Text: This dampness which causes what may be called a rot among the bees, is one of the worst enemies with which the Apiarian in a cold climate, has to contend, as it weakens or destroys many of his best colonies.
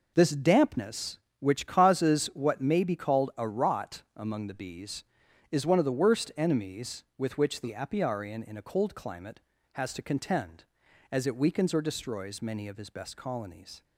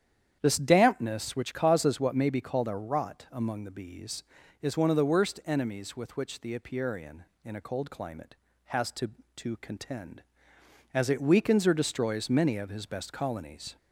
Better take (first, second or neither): first